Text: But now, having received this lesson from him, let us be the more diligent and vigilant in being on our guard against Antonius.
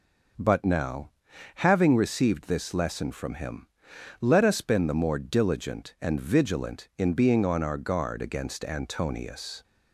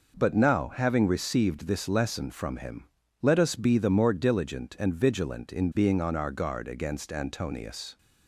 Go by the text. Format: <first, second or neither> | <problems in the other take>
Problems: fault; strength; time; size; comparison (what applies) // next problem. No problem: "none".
second | says "been" for "be"; at 4.6 s